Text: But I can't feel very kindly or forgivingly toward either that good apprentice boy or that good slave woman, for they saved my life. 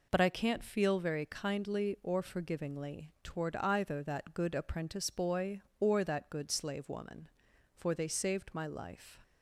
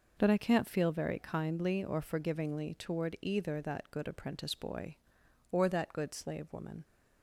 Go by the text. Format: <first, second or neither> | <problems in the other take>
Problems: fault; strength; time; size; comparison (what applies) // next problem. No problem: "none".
first | stops before "for they saved my life"; at 6.8 s